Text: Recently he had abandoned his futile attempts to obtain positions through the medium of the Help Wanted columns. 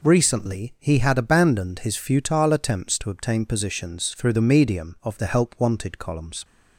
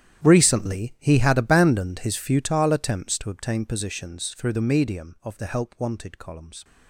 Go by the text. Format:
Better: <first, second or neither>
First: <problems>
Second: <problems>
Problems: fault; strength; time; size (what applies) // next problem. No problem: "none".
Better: first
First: none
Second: gets quieter; strong; throughout; 17 dB